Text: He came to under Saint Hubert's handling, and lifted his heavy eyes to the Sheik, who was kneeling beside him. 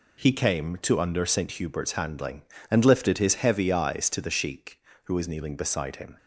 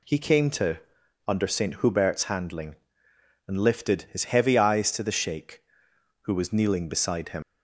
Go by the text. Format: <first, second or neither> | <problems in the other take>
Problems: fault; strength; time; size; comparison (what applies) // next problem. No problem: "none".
first | pauses between "to" and "under"; noticeable; at 0.7 s; 0.48 s long // leaves "him" unfinished; at 7.4 s; 125 ms